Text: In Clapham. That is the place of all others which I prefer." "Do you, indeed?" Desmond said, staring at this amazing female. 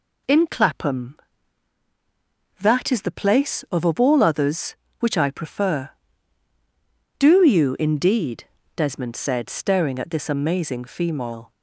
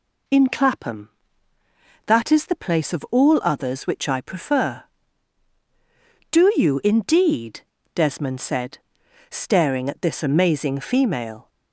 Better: second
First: says "of" twice; at 3.8 s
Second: none

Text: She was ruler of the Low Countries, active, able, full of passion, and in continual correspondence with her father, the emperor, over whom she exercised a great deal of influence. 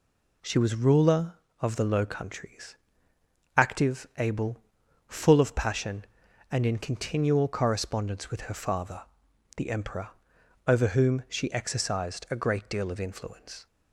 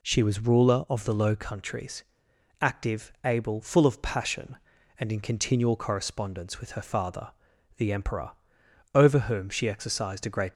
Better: first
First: none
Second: stops before "deal of influence"; at 10.5 s

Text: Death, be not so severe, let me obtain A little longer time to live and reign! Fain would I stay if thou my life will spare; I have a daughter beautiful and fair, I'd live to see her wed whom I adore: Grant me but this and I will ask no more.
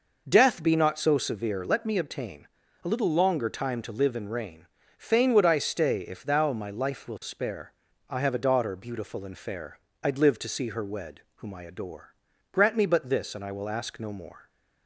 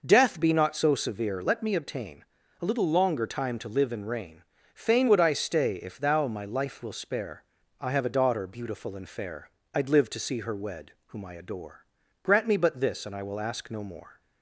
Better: neither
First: pauses between "obtain" and "A"; slight; at 2.4 s; 0.36 s long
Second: pauses between "obtain" and "A"; slight; at 2.2 s; 0.36 s long

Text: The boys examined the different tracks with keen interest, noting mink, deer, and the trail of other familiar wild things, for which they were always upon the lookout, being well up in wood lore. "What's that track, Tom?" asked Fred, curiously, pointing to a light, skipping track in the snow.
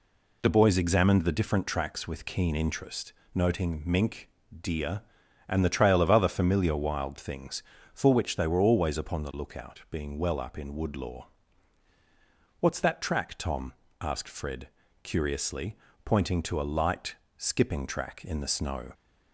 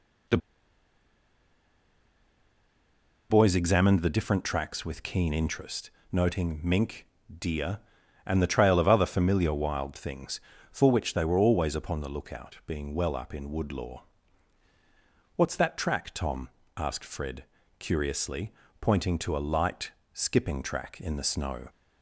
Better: first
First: none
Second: pauses between "The" and "boys"; strong; at 0.3 s; 2.9 s long

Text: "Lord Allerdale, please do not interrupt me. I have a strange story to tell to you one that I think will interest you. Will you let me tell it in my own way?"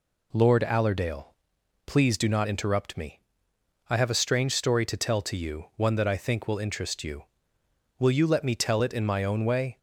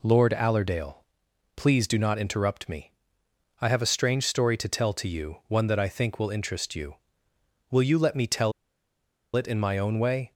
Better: first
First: none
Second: pauses between "tell" and "it"; noticeable; at 8.5 s; 0.83 s long

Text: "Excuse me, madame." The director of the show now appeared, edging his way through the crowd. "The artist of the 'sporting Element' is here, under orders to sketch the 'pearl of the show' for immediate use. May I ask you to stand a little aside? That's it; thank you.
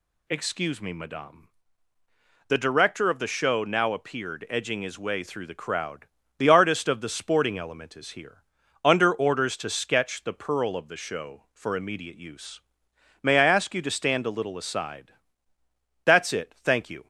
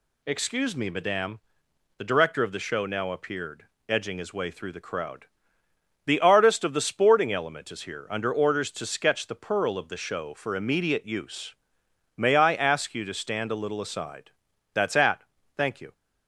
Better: first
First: none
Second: says "at" for "it"; at 14.9 s

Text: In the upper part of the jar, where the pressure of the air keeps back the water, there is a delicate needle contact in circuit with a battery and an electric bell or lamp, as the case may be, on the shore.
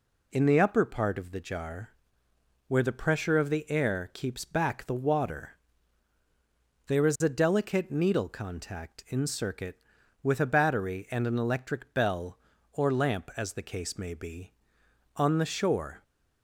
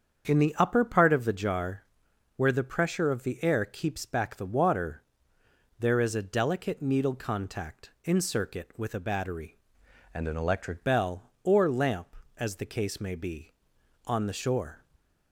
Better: first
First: none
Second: starts louder than the rest; strong; until 1.3 s; 7.5 dB // changes voice from "and" to "electric"; from 10.1 to 10.8 s; 0.7 s long // stays silent after the last word; slight; from 14.8 s on; 0.5 s long

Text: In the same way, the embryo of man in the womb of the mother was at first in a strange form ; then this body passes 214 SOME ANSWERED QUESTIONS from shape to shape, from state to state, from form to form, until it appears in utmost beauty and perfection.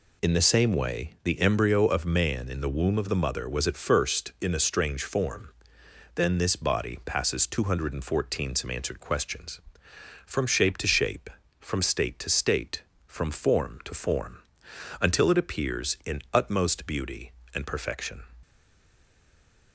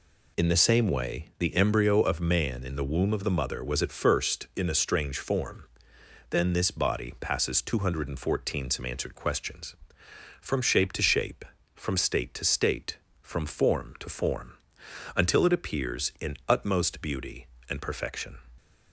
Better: second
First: stays silent after the last word; noticeable; from 18.4 s on; 1.3 s long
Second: none

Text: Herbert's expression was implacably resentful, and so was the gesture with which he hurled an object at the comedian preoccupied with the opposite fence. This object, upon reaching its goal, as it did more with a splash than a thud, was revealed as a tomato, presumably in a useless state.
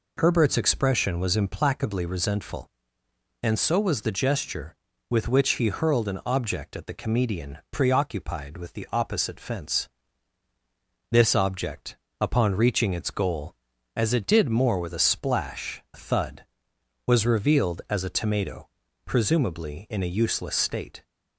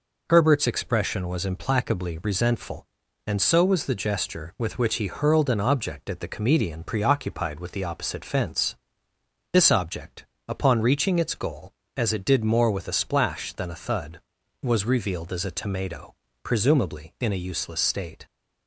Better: second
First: skips "than"; at 15.8 s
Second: none

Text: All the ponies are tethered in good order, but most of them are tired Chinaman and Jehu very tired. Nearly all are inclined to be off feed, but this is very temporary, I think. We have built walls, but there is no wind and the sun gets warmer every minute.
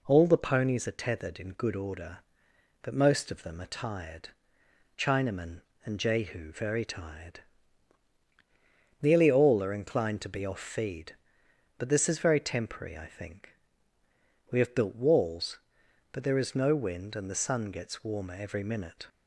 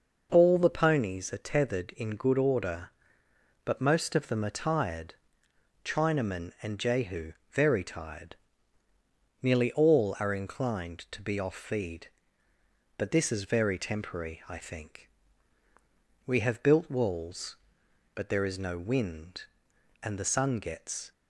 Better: first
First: pauses between "tired" and "Chinaman"; noticeable; at 4.2 s; 0.68 s long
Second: pauses between "tired" and "Chinaman"; noticeable; at 5.1 s; 0.68 s long // pauses between "Jehu" and "very"; slight; at 7.3 s; 0.18 s long // stops before "warmer every minute"; at 21.1 s

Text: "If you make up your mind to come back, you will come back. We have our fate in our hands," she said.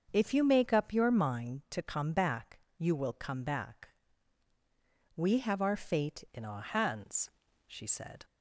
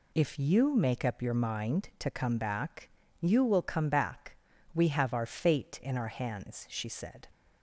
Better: second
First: starts louder than the rest; until 1.1 s; 6.5 dB // changes voice at "in"; from 6.3 s on; 1.9 s long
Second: none

